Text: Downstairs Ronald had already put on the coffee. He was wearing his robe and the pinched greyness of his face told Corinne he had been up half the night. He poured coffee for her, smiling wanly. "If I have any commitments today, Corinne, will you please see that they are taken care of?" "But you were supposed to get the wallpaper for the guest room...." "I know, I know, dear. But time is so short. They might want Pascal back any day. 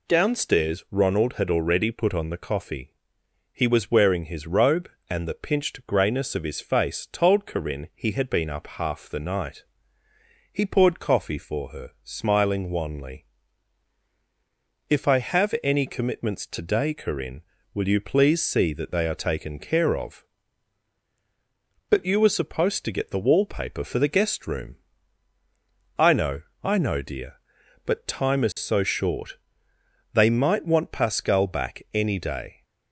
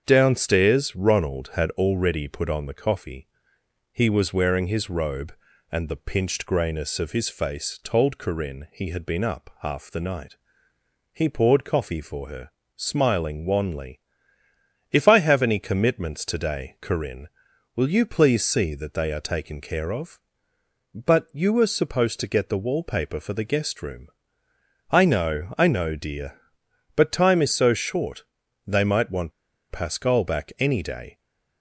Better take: first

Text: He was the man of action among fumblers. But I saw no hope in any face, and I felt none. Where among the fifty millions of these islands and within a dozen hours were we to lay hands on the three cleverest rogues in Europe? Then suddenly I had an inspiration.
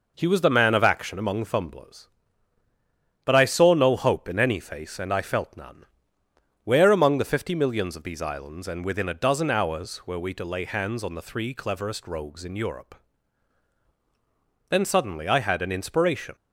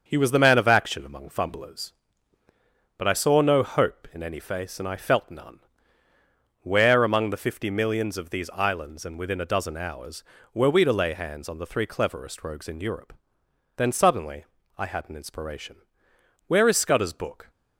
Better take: first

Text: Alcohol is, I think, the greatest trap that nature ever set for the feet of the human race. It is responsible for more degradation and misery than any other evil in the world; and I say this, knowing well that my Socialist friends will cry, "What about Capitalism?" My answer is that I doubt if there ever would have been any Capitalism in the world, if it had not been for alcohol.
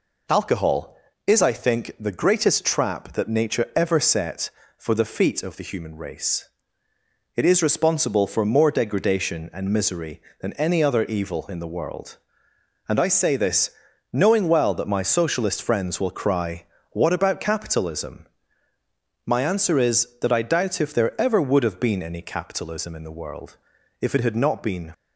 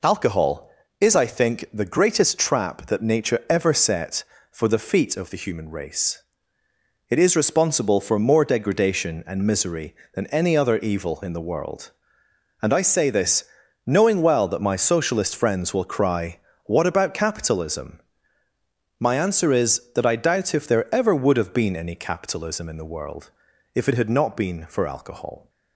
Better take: second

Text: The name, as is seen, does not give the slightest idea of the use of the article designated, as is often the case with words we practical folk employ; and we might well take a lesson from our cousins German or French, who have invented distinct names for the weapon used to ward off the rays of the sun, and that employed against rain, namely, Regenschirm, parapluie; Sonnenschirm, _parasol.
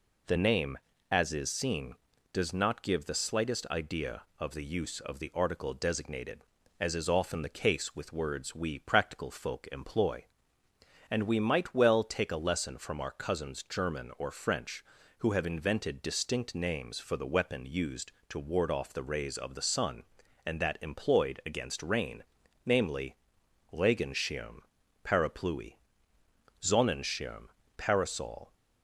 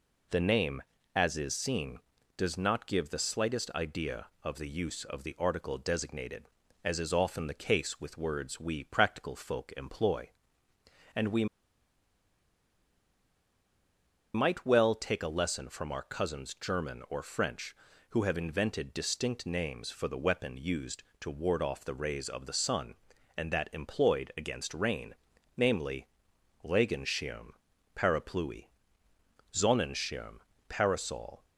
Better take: first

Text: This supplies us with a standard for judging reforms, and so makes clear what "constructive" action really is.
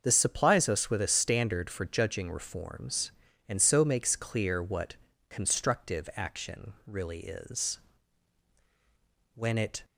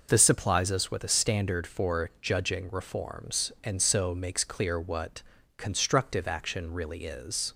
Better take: second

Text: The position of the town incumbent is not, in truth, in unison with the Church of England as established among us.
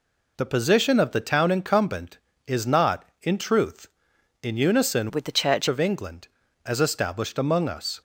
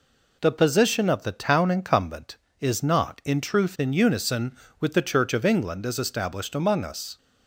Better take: second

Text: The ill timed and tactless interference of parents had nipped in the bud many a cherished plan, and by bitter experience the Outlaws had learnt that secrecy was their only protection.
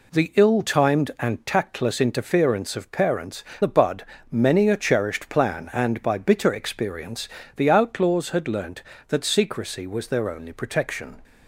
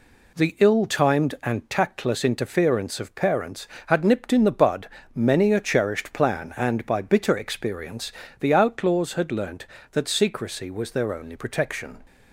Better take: second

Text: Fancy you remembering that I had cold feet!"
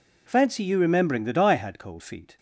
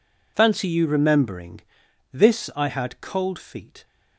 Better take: first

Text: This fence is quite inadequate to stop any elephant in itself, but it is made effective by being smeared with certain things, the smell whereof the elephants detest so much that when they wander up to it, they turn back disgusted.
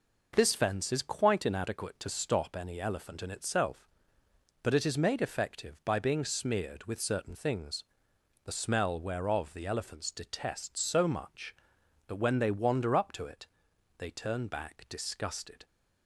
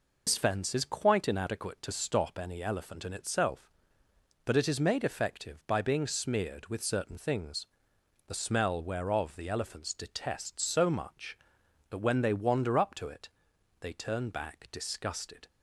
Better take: first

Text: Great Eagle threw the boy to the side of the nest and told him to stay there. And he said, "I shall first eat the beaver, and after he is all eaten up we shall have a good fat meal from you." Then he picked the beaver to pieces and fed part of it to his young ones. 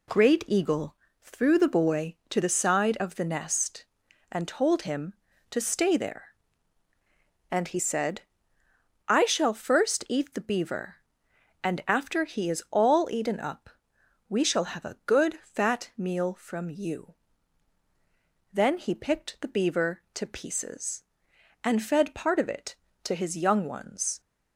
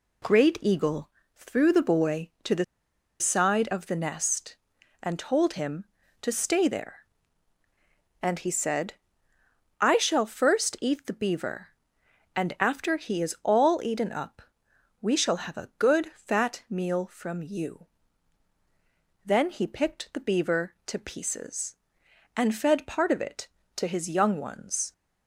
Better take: first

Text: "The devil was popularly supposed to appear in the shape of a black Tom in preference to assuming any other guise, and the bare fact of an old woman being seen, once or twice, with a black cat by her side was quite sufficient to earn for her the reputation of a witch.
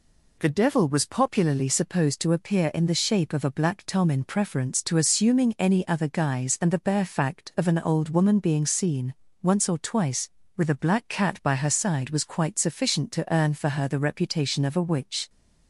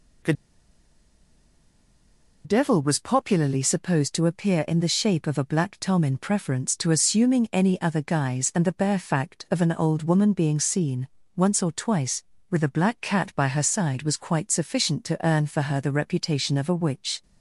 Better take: first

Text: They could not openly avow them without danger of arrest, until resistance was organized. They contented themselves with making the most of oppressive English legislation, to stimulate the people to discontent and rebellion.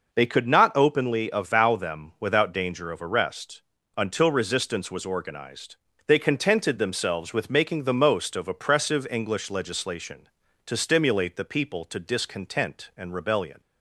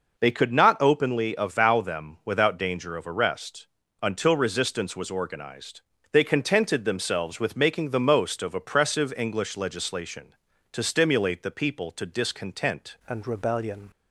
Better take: first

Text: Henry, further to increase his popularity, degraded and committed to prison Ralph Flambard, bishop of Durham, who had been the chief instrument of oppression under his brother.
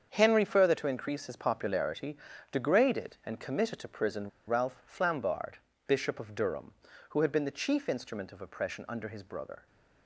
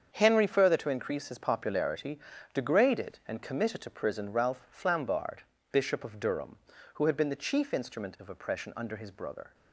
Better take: second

